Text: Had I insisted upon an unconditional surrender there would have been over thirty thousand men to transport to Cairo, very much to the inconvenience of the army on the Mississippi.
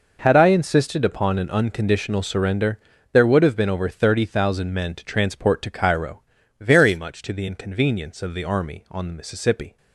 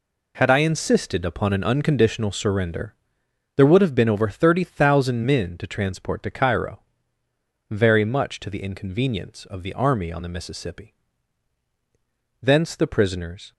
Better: first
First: pauses between "surrender" and "there"; slight; at 2.7 s; 0.36 s long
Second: pauses between "surrender" and "there"; noticeable; at 2.9 s; 0.62 s long // goes on to say "Thence the prisoners"; noticeable; from 12.4 s on; 1.1 s long

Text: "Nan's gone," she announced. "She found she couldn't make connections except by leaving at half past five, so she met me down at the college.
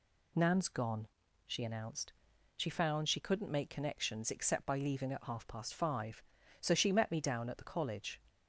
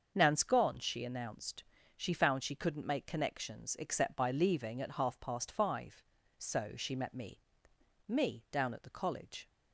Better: first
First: none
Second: starts louder than the rest; until 1.1 s; 6.5 dB // says "me" twice; at 8.0 s

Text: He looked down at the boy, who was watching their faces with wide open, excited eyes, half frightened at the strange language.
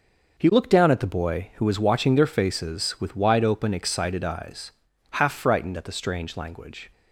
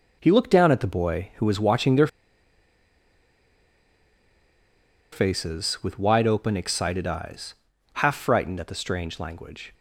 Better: first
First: none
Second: pauses between "their" and "faces"; strong; at 2.0 s; 3.0 s long

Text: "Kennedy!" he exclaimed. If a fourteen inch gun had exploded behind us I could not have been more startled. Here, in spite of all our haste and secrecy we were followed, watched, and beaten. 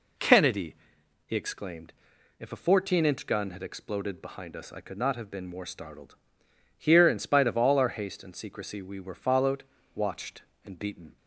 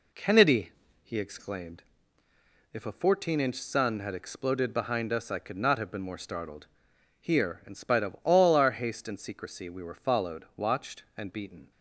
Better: first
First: none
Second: says "sun" for "gun"; at 3.6 s

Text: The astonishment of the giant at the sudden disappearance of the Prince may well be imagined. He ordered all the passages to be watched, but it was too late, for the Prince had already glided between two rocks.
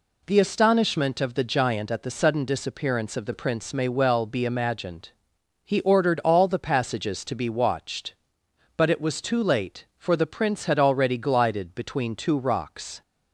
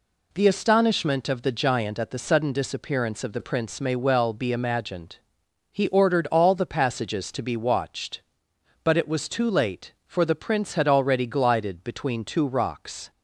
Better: neither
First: none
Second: none

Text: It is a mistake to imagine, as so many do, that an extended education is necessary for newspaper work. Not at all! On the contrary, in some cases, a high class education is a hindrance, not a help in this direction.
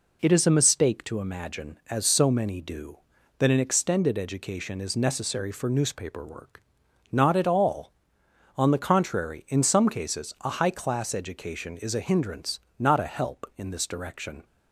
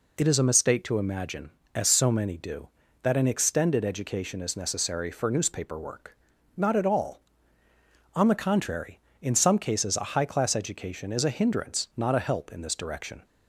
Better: neither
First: none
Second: none

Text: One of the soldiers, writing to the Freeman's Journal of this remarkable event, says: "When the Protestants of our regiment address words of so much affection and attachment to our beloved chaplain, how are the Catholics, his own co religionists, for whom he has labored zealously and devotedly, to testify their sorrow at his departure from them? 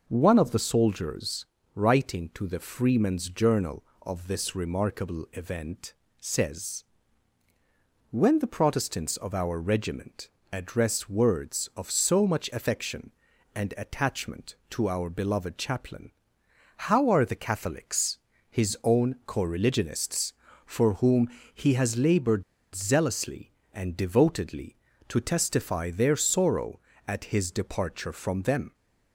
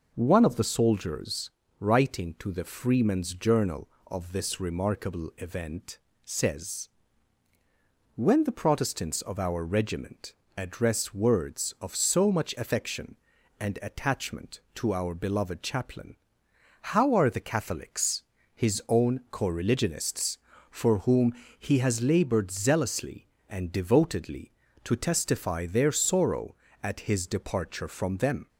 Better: second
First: pauses between "regiment" and "address"; slight; at 10.2 s; 0.24 s long // pauses between "whom" and "he"; slight; at 21.2 s; 0.24 s long // pauses between "labored" and "zealously"; slight; at 22.4 s; 0.32 s long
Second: pauses between "regiment" and "address"; slight; at 10.3 s; 0.24 s long // pauses between "whom" and "he"; slight; at 21.3 s; 0.24 s long

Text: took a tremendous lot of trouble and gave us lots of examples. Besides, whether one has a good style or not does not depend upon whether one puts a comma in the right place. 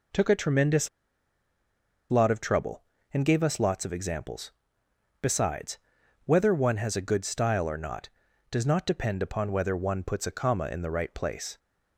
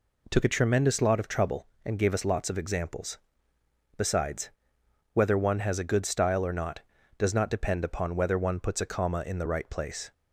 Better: second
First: pauses between "tremendous" and "lot"; at 0.8 s; 1.2 s long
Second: none

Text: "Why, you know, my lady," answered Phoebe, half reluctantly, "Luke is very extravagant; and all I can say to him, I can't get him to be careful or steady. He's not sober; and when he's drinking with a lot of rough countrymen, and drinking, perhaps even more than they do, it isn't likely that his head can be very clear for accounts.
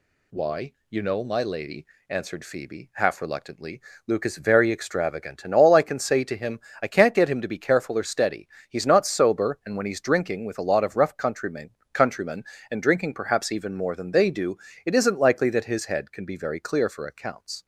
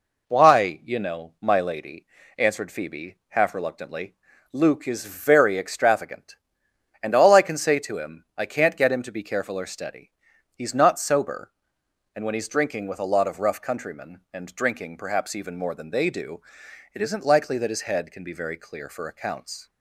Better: second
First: says "countrymen" twice; at 11.9 s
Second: none

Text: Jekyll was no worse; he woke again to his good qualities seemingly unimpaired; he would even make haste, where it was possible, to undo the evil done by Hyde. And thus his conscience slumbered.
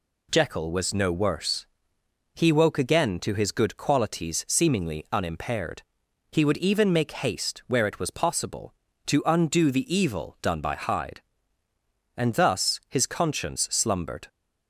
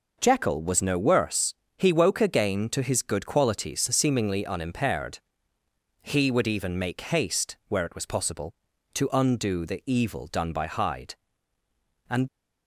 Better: first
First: none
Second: stops before "thus his conscience slumbered"; at 12.2 s

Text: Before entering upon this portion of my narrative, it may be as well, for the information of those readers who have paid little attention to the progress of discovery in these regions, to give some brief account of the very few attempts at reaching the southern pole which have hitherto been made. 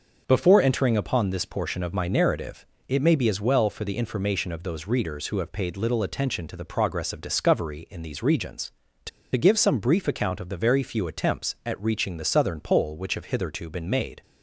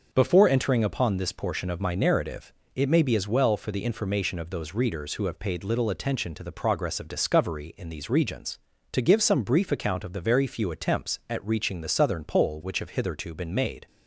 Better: second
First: starts louder than the rest; noticeable; until 1.2 s; 6 dB // pauses between "to" and "give"; slight; at 9.0 s; 0.25 s long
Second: starts louder than the rest; noticeable; until 1.1 s; 6 dB

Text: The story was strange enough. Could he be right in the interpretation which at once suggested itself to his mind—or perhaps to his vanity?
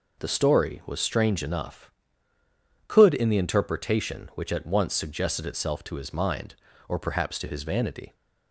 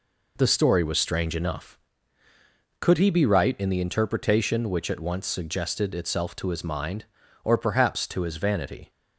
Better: second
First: skips "he be right"; at 3.1 s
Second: none

